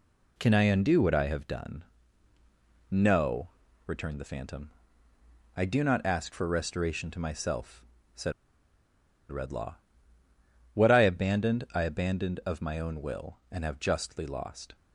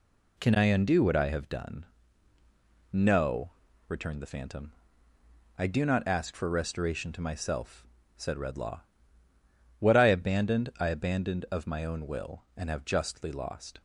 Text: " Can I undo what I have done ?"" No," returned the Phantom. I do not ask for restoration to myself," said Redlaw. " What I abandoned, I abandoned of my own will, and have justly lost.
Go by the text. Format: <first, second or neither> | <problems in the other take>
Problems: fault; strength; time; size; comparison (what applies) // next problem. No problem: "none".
second | pauses between "said" and "Redlaw"; at 8.3 s; 0.98 s long